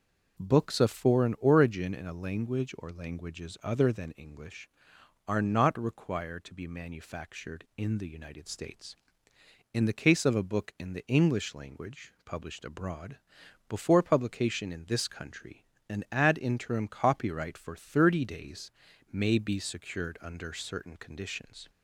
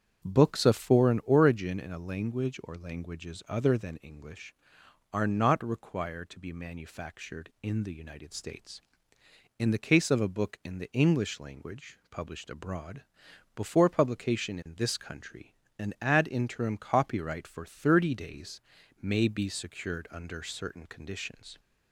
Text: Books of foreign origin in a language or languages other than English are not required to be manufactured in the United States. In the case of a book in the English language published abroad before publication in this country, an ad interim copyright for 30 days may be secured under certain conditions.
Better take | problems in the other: first | starts louder than the rest; strong; until 1.4 s; 8 dB // pauses between "abroad" and "before"; noticeable; at 13.0 s; 0.54 s long; noticeable in the first // pauses between "days" and "may"; at 18.6 s; 0.42 s long; also in the first

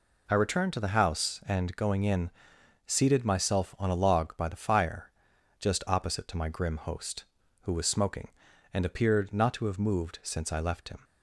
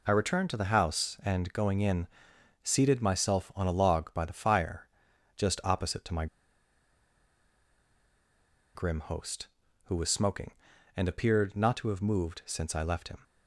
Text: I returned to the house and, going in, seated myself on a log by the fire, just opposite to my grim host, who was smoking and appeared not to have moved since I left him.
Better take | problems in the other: first | pauses between "my" and "grim"; strong; at 6.2 s; 2.4 s long

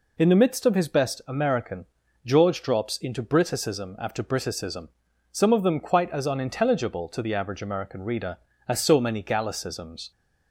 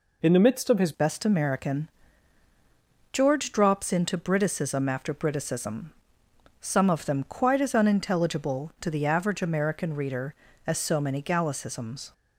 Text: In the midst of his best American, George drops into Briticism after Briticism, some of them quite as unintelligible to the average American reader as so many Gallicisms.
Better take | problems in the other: first | changes voice at "best"; from 0.9 s on; 11.2 s long

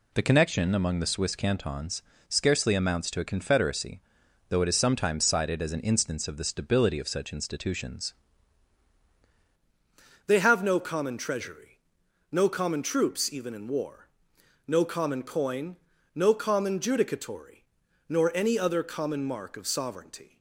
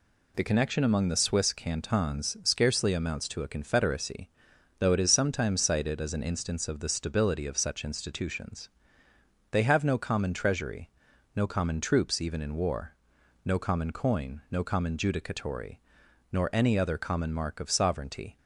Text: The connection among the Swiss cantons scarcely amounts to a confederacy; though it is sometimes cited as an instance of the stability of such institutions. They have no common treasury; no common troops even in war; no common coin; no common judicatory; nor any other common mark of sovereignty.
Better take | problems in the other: second | pauses between "cantons" and "scarcely"; slight; at 2.0 s; 0.26 s long // changes voice at "They"; from 10.2 s on; 10.1 s long

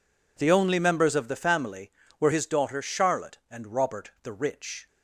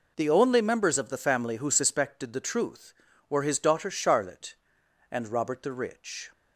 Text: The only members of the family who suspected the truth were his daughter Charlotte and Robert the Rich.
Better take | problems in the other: second | skips "who suspected the truth"; at 2.0 s

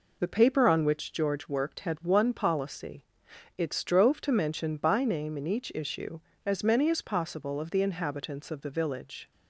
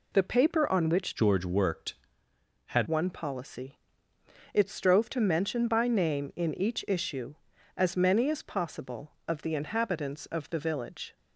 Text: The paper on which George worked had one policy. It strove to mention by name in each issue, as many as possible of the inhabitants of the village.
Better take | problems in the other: first | changes voice from "George" to "had"; from 1.1 to 2.8 s; 1.7 s long

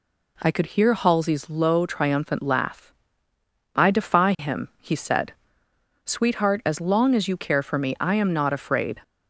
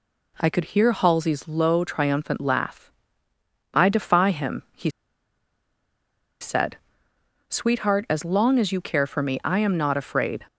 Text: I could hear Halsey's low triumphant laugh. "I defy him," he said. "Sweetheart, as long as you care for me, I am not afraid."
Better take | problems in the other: first | pauses between "he" and "said"; strong; at 4.8 s; 1.5 s long

